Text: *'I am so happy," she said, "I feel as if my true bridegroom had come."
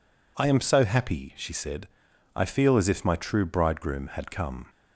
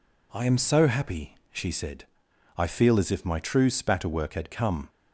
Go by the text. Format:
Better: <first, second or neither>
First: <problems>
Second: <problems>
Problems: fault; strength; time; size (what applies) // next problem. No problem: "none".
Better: first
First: none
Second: says "spatterwork" for "bridegroom"; at 3.6 s